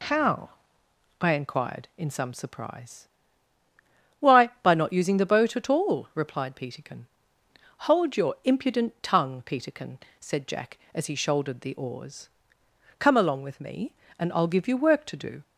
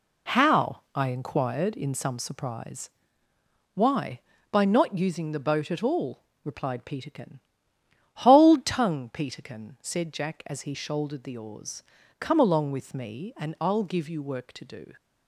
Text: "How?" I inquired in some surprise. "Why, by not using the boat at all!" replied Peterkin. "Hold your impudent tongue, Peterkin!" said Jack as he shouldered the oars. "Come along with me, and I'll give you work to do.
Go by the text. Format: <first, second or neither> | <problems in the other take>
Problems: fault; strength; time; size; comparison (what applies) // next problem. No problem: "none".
first | skips "your impudent"; at 8.6 s